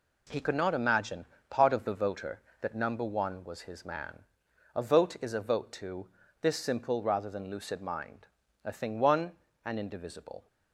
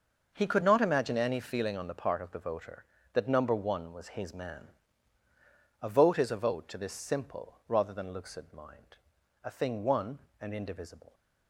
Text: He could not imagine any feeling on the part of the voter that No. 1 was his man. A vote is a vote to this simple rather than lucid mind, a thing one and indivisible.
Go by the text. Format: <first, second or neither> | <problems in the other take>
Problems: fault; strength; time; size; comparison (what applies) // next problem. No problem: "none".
second | skips "any feeling on the"; at 1.3 s // pauses between "to" and "this"; slight; at 6.0 s; 0.34 s long